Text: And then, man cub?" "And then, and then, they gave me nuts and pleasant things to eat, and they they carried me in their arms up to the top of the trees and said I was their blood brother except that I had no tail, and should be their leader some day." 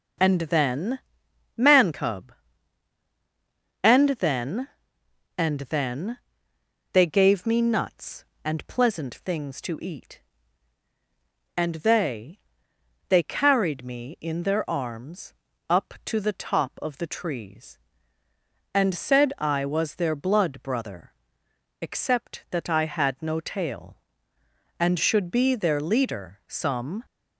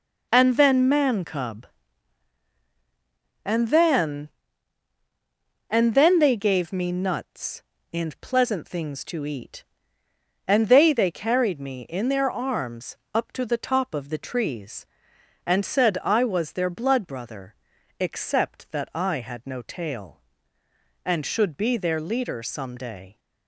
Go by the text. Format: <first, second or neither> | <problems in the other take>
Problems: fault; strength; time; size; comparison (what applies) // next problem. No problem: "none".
second | pauses between "they" and "they"; noticeable; at 12.3 s; 0.68 s long // pauses between "arms" and "up"; slight; at 15.3 s; 0.36 s long; slight in the second // pauses between "brother" and "except"; noticeable; at 21.1 s; 0.68 s long; also in the second // stops before "day"; at 27.0 s